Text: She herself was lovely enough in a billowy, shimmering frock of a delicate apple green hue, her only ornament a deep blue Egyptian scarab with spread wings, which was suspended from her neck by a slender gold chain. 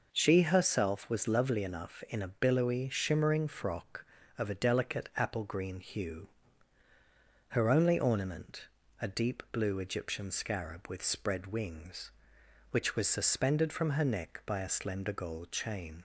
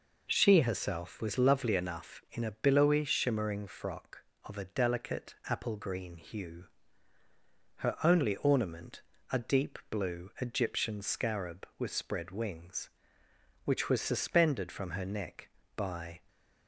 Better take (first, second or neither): first